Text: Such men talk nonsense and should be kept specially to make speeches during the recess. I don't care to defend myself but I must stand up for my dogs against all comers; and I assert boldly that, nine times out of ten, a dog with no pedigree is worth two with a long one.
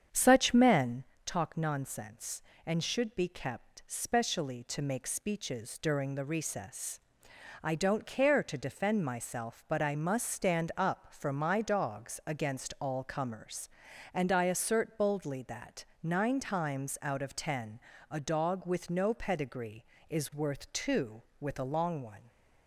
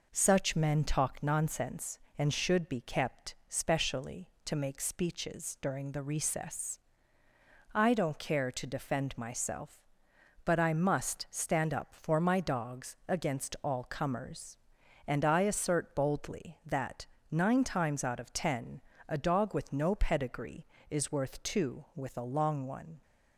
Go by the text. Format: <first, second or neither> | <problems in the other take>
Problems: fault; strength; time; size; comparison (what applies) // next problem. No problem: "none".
second | starts louder than the rest; strong; until 1.2 s; 8 dB // pauses between "men" and "talk"; slight; at 1.0 s; 0.20 s long